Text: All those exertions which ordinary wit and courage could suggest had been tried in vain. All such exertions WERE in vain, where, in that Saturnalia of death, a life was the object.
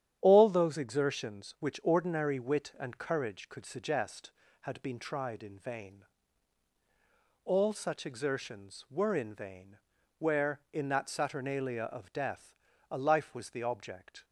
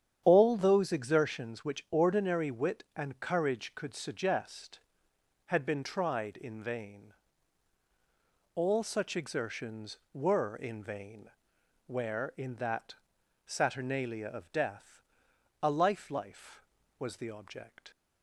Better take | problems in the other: first | starts louder than the rest; strong; until 1.2 s; 9 dB; strong in the first // pauses between "that" and "Saturnalia"; noticeable; at 12.9 s; 0.50 s long // says "life" twice; at 16.1 s

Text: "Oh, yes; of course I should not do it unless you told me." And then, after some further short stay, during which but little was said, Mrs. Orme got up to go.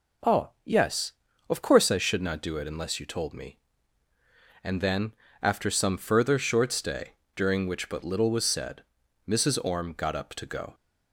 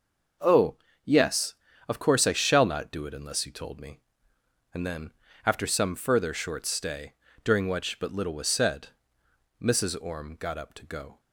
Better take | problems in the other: first | says "shall" for "should"; at 2.3 s

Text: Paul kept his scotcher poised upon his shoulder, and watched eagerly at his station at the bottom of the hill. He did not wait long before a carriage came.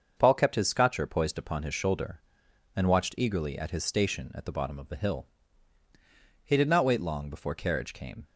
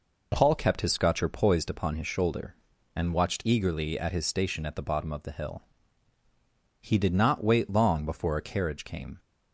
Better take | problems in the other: second | starts louder than the rest; until 1.1 s; 6.5 dB // skips "a"; at 7.5 s

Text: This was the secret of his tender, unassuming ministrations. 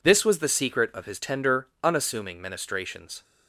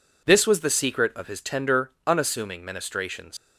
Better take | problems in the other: first | leaves "ministrations" unfinished; at 3.3 s; 95 ms

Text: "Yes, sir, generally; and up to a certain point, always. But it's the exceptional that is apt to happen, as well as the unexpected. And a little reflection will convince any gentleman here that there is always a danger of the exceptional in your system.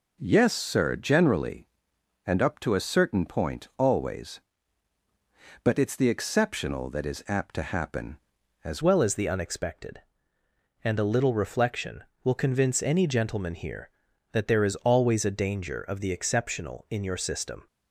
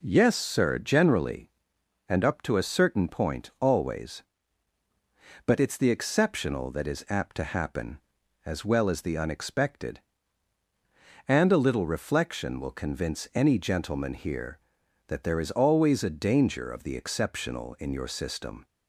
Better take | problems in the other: second | changes voice at "well"; from 8.8 s on; 8.8 s long

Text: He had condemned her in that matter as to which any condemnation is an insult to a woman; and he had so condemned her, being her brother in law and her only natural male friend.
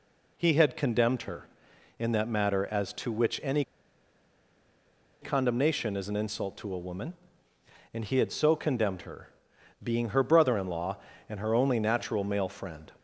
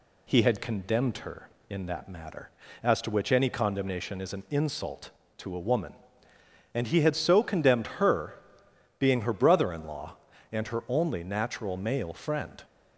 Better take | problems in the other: second | pauses between "any" and "condemnation"; strong; at 3.6 s; 1.5 s long

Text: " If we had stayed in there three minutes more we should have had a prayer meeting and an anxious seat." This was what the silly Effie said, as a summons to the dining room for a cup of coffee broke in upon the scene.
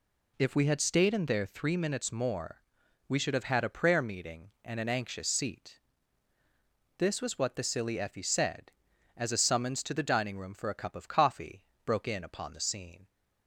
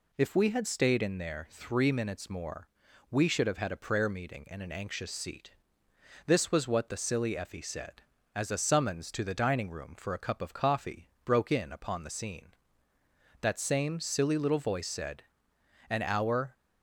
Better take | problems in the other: first | pauses between "more" and "we"; at 2.6 s; 0.42 s long; noticeable in the first // pauses between "coffee" and "broke"; slight; at 11.0 s; 0.16 s long; slight in the first // goes on to say "That same silly little voice said an hour"; strong; from 13.4 s on; 3.1 s long

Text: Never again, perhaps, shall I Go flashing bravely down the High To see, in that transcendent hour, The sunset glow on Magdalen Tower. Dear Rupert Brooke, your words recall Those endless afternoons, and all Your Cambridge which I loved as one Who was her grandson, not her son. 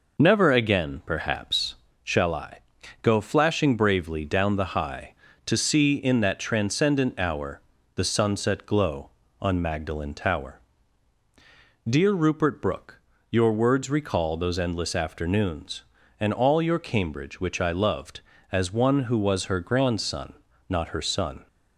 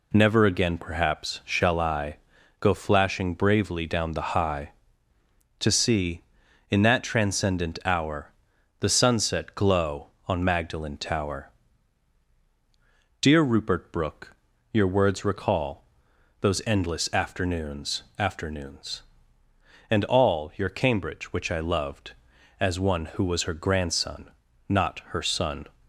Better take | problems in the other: first | pauses between "I" and "Go"; at 2.1 s; 0.44 s long; also in the first // pauses between "recall" and "Those"; noticeable; at 15.8 s; 0.56 s long // says "afternoons" twice; at 18.1 s

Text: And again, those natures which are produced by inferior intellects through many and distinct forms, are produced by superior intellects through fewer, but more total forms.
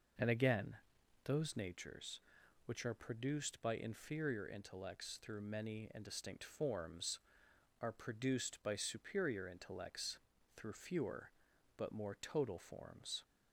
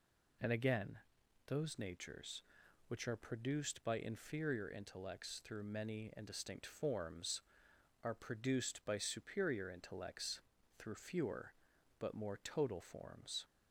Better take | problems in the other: second | starts louder than the rest; noticeable; until 1.8 s; 5.5 dB // pauses between "intellects" and "through"; at 10.1 s; 0.38 s long; also in the second

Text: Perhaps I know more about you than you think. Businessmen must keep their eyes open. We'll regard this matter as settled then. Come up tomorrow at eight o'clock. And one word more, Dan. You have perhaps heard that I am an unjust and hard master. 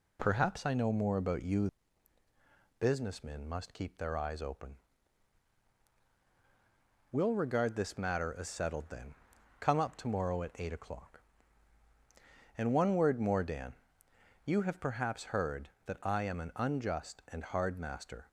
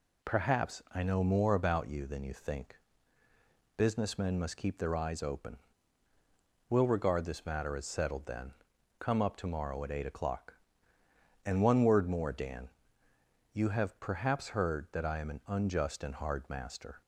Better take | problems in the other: second | skips "than you think"; at 2.2 s

